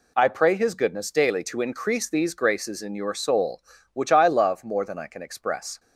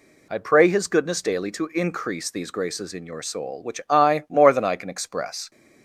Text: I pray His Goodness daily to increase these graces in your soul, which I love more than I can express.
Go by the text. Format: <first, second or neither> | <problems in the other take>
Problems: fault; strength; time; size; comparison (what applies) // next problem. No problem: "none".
first | skips "love"; at 4.2 s